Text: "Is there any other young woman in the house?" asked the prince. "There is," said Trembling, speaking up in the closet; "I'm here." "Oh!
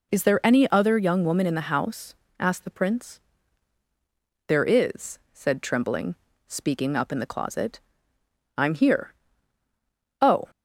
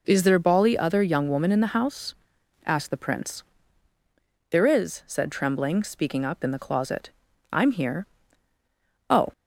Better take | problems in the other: first | says "bali" for "any"; at 0.3 s

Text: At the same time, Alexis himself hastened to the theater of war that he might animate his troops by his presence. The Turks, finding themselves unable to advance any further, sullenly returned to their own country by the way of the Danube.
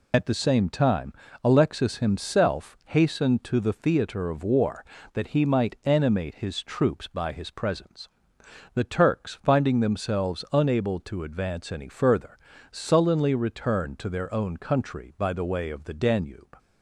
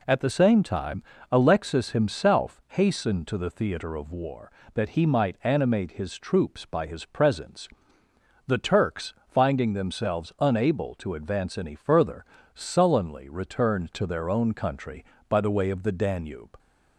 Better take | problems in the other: second | loses the start of "At"; at 0.1 s; 60 ms

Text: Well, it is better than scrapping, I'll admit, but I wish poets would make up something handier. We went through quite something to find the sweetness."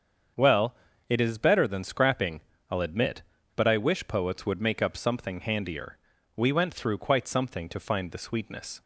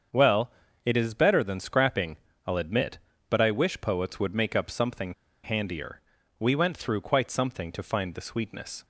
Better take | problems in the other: first | starts louder than the rest; strong; until 1.4 s; 7 dB; strong in the first // pauses between "something" and "handier"; slight; at 5.1 s; 0.30 s long

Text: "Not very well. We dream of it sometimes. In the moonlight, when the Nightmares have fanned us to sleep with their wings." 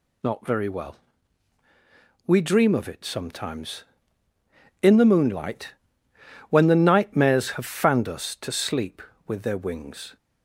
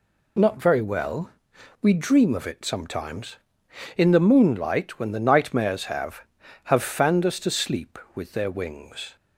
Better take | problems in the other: first | says "have" twice; at 6.6 s

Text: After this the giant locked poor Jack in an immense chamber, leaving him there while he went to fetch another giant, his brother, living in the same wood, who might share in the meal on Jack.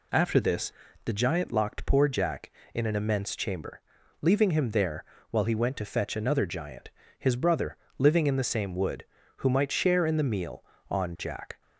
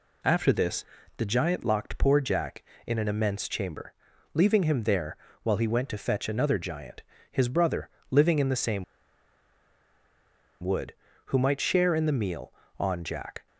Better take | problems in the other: first | pauses between "this" and "the"; slight; at 0.8 s; 0.32 s long; slight in the first // pauses between "there" and "while"; slight; at 5.1 s; 0.28 s long; slight in the first // pauses between "same" and "wood"; strong; at 8.8 s; 1.7 s long

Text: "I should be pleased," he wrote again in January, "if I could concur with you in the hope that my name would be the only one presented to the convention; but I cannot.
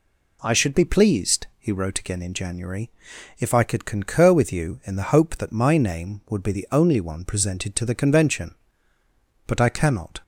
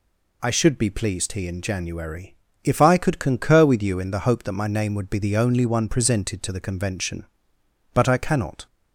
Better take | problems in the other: first | skips "wrote again"; at 1.4 s

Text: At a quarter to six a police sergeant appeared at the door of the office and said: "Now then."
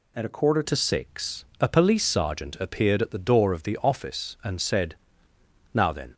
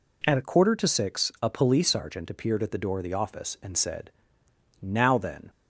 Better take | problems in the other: second | changes voice at "to"; from 0.6 s on; 5.5 s long // pauses between "six" and "a"; slight; at 1.4 s; 0.16 s long

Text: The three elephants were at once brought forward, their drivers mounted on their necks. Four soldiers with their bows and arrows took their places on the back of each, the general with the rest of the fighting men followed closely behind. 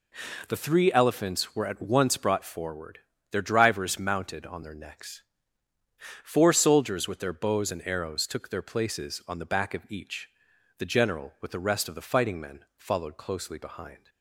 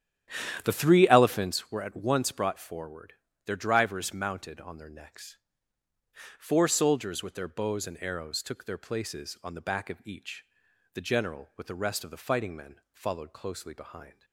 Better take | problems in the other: first | starts louder than the rest; strong; until 1.6 s; 10.5 dB

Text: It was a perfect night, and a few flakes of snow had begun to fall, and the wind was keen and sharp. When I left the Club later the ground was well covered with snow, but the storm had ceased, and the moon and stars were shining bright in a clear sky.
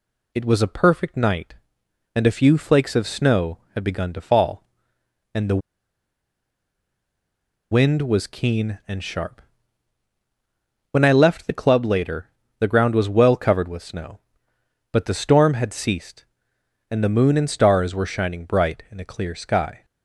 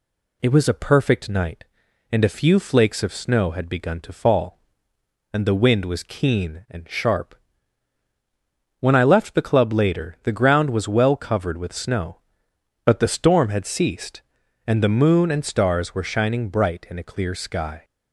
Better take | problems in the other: second | pauses between "the" and "wind"; strong; at 5.6 s; 2.1 s long // pauses between "later" and "the"; slight; at 12.2 s; 0.32 s long

